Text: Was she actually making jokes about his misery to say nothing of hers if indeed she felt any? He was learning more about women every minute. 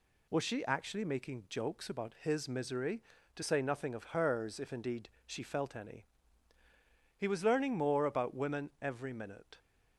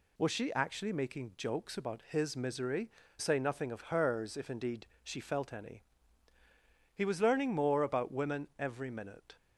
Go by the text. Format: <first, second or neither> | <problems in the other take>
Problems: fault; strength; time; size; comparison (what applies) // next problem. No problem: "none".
first | skips "to"; at 3.0 s // pauses between "indeed" and "she"; slight; at 4.8 s; 0.16 s long; slight in the first